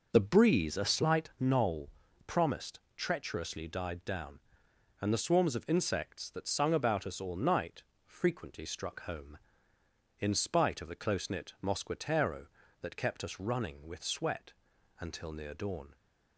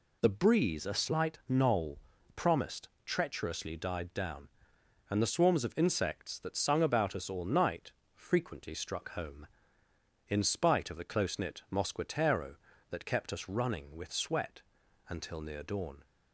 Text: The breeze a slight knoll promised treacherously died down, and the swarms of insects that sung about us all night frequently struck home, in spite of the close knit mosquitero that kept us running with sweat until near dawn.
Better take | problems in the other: second | starts louder than the rest; noticeable; until 1.4 s; 5.5 dB // pauses between "knoll" and "promised"; at 1.8 s; 0.38 s long; also in the second // pauses between "promised" and "treacherously"; slight; at 2.7 s; 0.16 s long; slight in the second // pauses between "night" and "frequently"; slight; at 7.8 s; 0.22 s long; slight in the second // pauses between "sweat" and "until"; noticeable; at 14.5 s; 0.48 s long; noticeable in the second

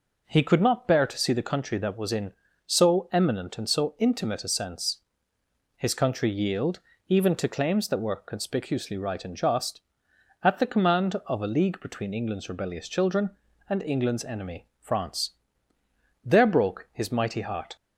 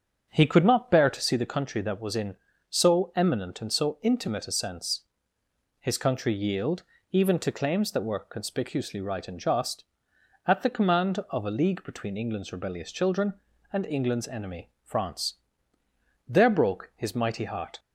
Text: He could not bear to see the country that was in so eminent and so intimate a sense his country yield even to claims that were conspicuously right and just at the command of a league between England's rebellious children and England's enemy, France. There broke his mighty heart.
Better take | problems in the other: first | starts louder than the rest; strong; until 1.3 s; 7.5 dB // pauses between "sense" and "his"; noticeable; at 5.0 s; 0.78 s long; noticeable in the first // pauses between "yield" and "even"; slight; at 6.8 s; 0.28 s long; slight in the first

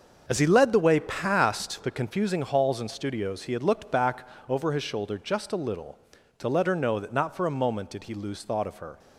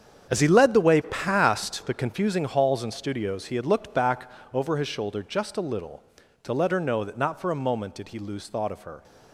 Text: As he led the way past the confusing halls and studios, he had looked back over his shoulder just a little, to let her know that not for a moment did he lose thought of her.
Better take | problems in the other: first | gets quieter; strong; throughout; 12.5 dB // starts louder than the rest; strong; until 1.3 s; 8 dB; also in the first // pauses between "back" and "over"; slight; at 4.2 s; 0.24 s long; slight in the first

